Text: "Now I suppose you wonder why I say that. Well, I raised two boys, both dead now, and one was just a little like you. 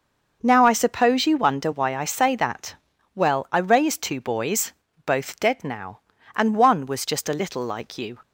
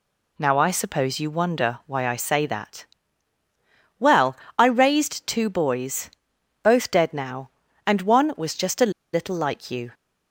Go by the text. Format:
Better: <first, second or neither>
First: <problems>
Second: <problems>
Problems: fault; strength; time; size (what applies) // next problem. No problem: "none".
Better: first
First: none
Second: pauses between "a" and "little"; slight; at 8.9 s; 0.21 s long